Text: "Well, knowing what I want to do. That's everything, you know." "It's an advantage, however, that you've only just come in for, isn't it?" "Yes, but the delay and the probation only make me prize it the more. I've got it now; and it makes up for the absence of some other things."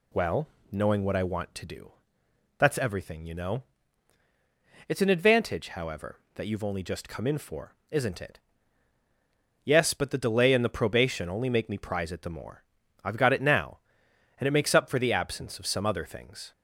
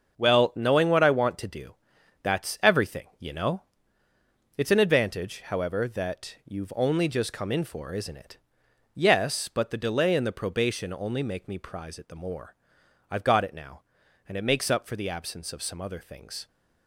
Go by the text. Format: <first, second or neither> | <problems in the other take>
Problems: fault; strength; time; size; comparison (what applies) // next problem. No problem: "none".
first | gets quieter; strong; throughout; 9 dB